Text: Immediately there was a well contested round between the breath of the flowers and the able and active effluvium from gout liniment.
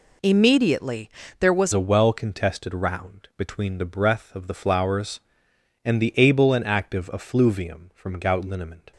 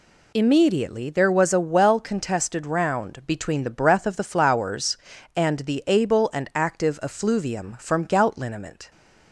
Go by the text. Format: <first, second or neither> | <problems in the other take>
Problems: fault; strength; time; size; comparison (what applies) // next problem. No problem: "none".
second | pauses between "Immediately" and "there"; slight; at 1.0 s; 0.30 s long // changes voice at "a"; from 1.7 s on; 7.2 s long